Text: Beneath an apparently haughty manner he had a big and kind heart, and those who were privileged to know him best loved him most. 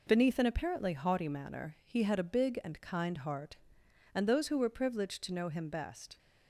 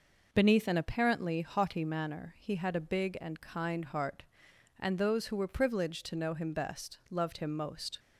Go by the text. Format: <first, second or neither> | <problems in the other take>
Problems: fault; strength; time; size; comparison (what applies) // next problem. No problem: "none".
second | stops before "loved him most"; at 6.1 s